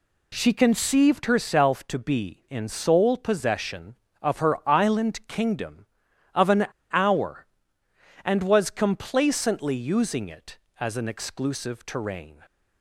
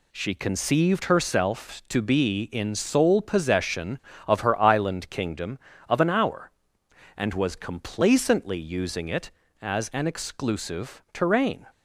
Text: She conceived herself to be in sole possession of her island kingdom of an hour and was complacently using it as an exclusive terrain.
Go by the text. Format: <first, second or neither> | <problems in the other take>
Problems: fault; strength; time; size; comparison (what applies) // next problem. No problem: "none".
second | pauses between "an" and "hour"; slight; at 6.6 s; 0.26 s long